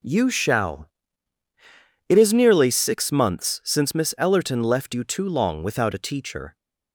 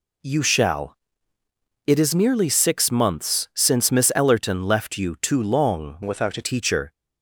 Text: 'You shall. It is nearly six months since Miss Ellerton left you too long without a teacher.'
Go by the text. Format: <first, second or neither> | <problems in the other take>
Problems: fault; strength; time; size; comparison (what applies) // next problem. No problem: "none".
first | changes voice from "without" to "a"; from 6.0 to 6.4 s; 0.4 s long